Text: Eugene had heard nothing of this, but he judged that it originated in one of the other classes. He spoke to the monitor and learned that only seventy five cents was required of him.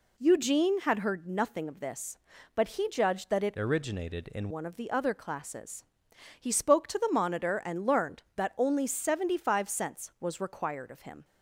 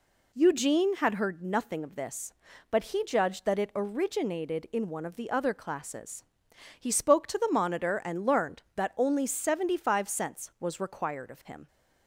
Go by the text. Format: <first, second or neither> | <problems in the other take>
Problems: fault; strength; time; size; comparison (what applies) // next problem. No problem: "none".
second | changes voice from "originated" to "in"; from 3.5 to 4.4 s; 0.9 s long